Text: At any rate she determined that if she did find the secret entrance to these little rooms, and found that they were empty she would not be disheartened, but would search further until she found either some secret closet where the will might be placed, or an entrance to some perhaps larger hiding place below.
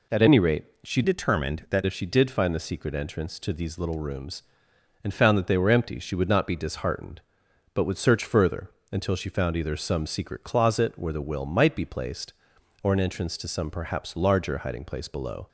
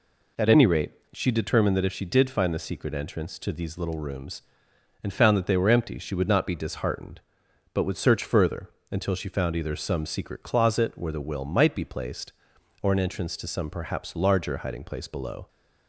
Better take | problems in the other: second | pauses between "rate" and "she"; slight; at 0.6 s; 0.20 s long; slight in the second // changes voice from "determined" to "that"; from 1.0 to 1.8 s; 0.8 s long // pauses between "further" and "until"; slight; at 8.6 s; 0.22 s long; slight in the second

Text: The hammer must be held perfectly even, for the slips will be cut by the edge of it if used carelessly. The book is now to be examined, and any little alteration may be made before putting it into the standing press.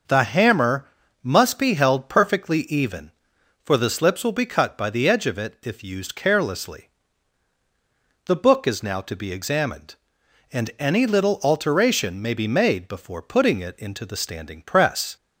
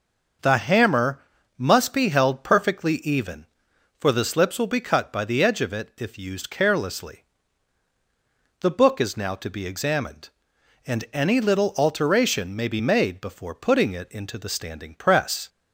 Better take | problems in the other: neither | pauses between "hammer" and "must"; slight; the same in both

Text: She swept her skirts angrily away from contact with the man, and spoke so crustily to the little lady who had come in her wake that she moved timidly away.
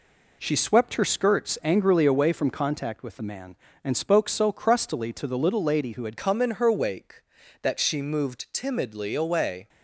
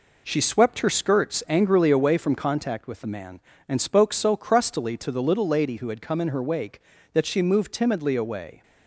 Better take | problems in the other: second | changes voice at "come"; from 6.1 s on; 3.5 s long

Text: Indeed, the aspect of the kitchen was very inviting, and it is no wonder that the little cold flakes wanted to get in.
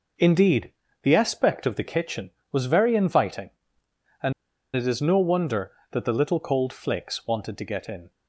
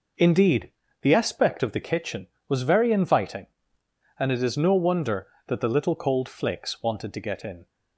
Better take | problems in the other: second | pauses between "and" and "it"; at 4.3 s; 0.43 s long

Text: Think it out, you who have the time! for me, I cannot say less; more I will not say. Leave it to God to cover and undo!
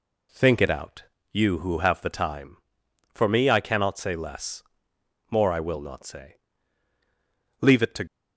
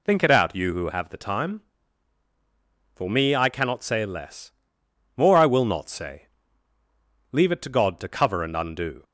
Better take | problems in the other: second | stops before "God to cover and undo"; at 8.0 s

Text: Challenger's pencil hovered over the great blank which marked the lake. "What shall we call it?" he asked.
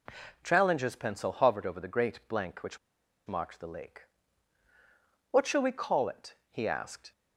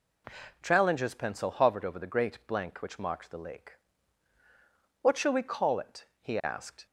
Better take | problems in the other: second | pauses between "which" and "marked"; noticeable; at 2.7 s; 0.49 s long

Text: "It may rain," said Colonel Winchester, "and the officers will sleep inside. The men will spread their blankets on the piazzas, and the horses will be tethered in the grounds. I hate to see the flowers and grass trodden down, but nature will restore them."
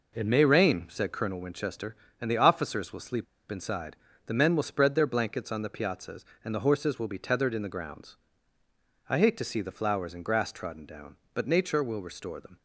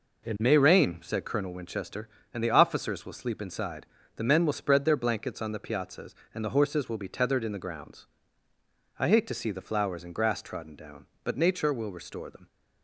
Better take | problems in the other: second | pauses between "sleep" and "inside"; slight; at 3.2 s; 0.25 s long

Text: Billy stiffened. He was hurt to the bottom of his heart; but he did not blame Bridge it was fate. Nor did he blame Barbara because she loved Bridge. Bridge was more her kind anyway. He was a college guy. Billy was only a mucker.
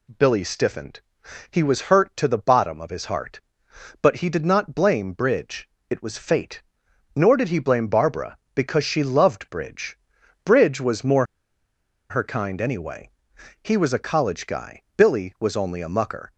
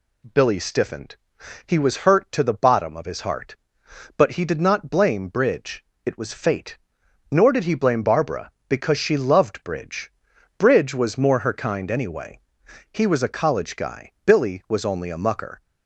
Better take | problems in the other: second | pauses between "Bridge" and "it"; slight; at 5.6 s; 0.22 s long; slight in the second // pauses between "more" and "her"; noticeable; at 11.2 s; 0.85 s long

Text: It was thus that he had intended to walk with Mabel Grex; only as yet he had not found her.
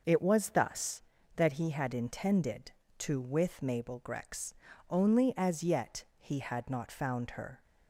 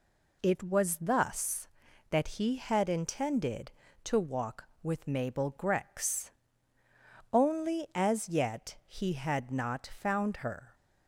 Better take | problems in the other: second | skips "walk"; at 3.2 s // pauses between "yet" and "he"; slight; at 6.0 s; 0.16 s long

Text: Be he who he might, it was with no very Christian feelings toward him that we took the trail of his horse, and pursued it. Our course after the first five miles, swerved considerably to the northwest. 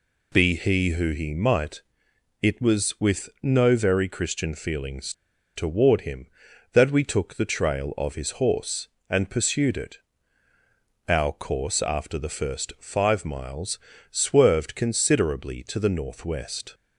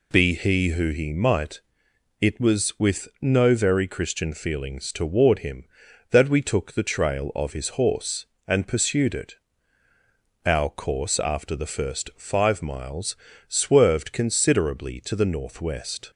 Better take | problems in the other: second | pauses between "feelings" and "toward"; at 5.1 s; 0.42 s long

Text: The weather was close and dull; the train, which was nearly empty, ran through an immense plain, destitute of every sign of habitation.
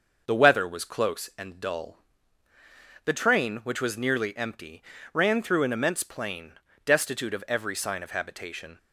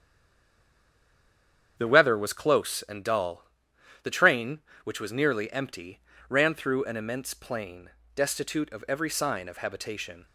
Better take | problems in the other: first | stays silent before the first word; noticeable; until 1.7 s; 1.7 s long // starts louder than the rest; strong; until 2.7 s; 8.5 dB

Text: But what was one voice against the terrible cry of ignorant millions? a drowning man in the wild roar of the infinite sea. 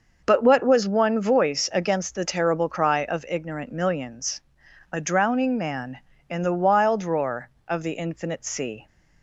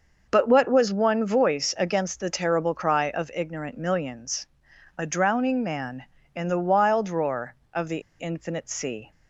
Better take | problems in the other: first | pauses between "the" and "infinite"; slight; at 7.9 s; 0.19 s long

